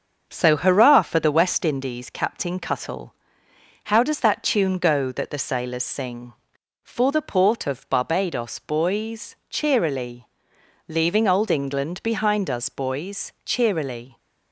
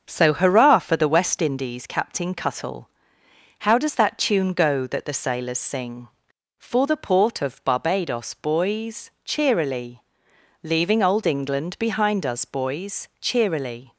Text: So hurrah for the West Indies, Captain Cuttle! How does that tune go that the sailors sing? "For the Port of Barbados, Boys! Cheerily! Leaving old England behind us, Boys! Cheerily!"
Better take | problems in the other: neither | starts louder than the rest; the same in both

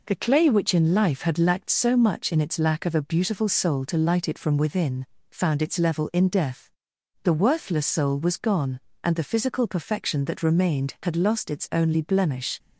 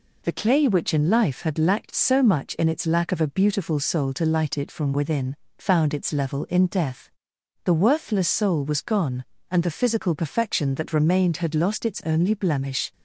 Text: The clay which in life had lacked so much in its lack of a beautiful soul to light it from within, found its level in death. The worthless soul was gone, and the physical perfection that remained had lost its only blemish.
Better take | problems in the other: neither | none

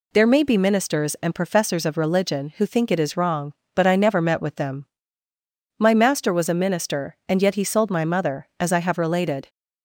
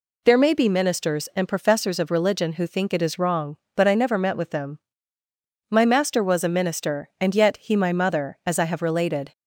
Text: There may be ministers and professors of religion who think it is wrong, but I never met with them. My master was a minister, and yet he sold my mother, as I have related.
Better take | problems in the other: first | skips "sold"; at 7.7 s

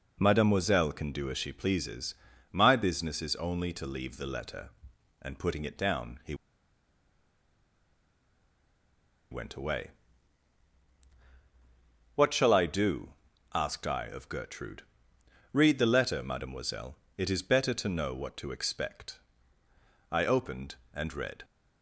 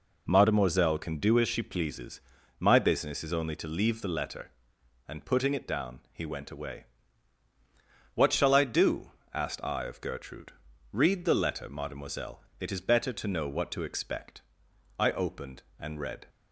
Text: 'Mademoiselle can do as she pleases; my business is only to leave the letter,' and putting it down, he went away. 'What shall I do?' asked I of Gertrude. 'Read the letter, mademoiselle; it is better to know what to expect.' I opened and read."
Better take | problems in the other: second | pauses between "he" and "went"; strong; at 6.3 s; 2.9 s long

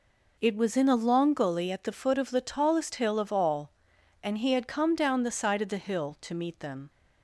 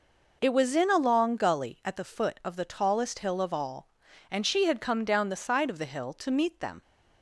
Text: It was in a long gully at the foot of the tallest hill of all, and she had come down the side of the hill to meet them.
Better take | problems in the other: second | says "he" for "she"; at 4.3 s

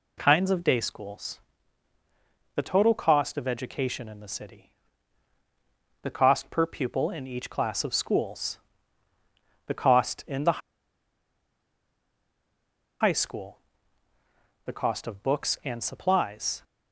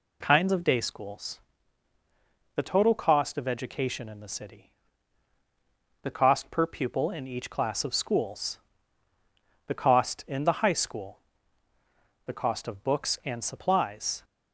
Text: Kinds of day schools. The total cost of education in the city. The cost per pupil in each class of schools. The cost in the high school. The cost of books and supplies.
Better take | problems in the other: second | pauses between "the" and "high"; strong; at 10.5 s; 2.4 s long

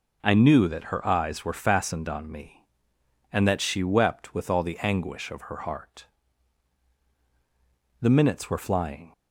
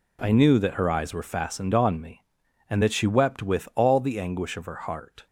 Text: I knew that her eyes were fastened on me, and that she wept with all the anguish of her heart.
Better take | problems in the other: second | goes on to say "The minutes were flying"; noticeable; from 8.0 s on; 1.1 s long

